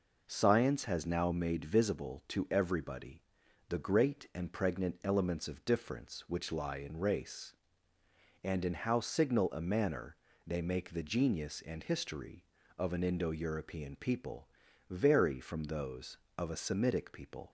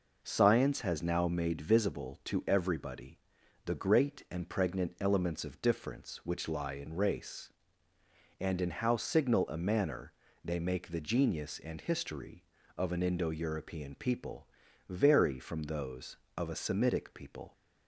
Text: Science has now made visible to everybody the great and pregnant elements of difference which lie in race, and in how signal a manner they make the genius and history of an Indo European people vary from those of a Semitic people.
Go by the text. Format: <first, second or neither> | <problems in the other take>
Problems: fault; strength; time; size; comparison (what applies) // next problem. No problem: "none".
neither | pauses between "everybody" and "the"; noticeable; the same in both // pauses between "manner" and "they"; slight; the same in both // pauses between "people" and "vary"; the same in both